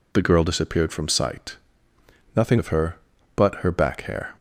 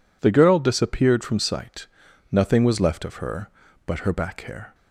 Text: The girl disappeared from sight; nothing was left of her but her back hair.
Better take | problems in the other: second | skips "was left"; at 2.5 s

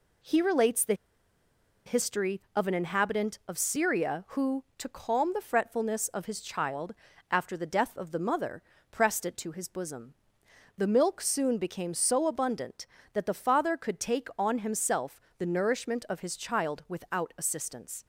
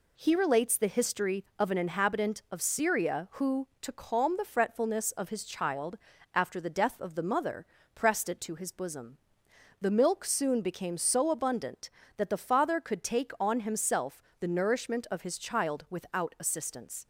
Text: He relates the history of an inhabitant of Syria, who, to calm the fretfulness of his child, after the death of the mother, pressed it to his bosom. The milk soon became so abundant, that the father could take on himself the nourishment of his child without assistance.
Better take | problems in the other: second | pauses between "the" and "history"; noticeable; at 0.9 s; 0.92 s long // pauses between "himself" and "the"; slight; at 15.2 s; 0.16 s long; slight in the second

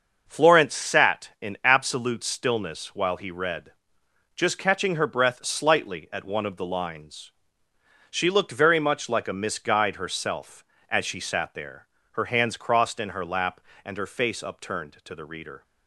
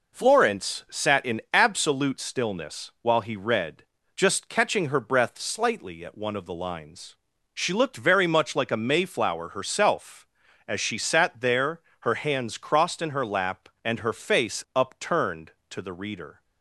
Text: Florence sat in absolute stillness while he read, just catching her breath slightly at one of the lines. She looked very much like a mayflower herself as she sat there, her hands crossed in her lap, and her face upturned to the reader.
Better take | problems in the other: second | starts louder than the rest; noticeable; until 1.2 s; 6 dB // says "misguide" for "mayflower"; at 9.3 s

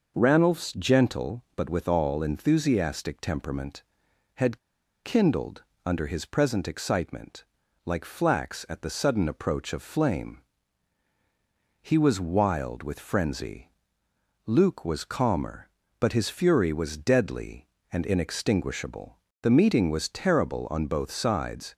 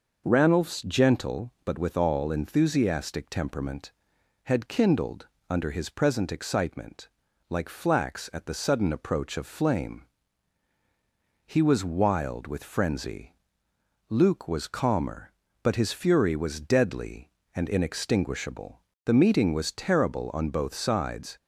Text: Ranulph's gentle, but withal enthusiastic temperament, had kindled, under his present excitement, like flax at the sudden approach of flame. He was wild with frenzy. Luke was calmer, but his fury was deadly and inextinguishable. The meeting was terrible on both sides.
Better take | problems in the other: second | pauses between "had" and "kindled"; at 4.5 s; 0.45 s long

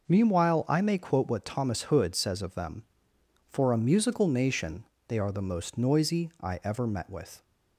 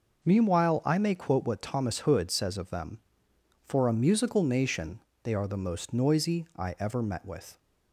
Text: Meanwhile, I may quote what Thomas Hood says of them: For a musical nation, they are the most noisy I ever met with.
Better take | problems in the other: neither | none

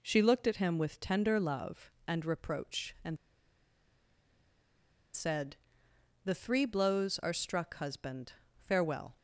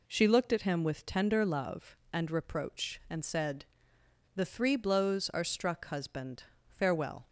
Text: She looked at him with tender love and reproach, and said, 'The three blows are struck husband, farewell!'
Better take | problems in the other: second | pauses between "and" and "said"; strong; at 3.1 s; 1.9 s long

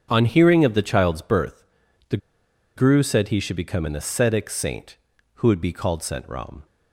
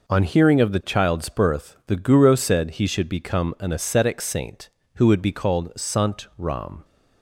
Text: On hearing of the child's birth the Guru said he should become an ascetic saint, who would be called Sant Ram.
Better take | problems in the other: second | starts louder than the rest; strong; until 1.1 s; 7 dB // pauses between "birth" and "the"; noticeable; at 1.6 s; 0.46 s long // pauses between "the" and "Guru"; noticeable; at 2.1 s; 0.59 s long

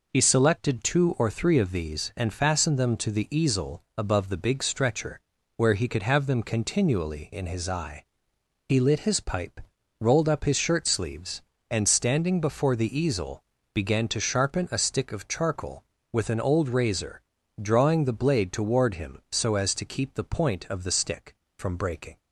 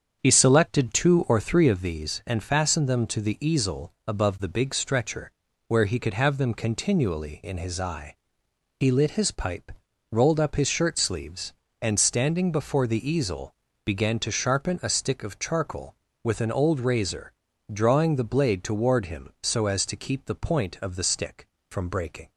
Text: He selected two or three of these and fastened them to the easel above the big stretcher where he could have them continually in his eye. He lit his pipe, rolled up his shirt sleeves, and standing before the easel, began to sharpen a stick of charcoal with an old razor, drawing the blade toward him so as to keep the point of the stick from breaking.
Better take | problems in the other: first | starts louder than the rest; strong; until 1.8 s; 7.5 dB // pauses between "stretcher" and "where"; slight; at 5.3 s; 0.36 s long; slight in the first

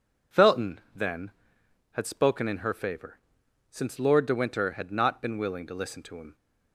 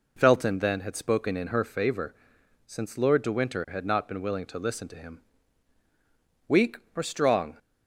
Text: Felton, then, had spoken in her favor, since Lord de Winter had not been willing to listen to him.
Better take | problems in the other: first | goes on to say "Weak or strong"; noticeable; from 6.4 s on; 1.1 s long

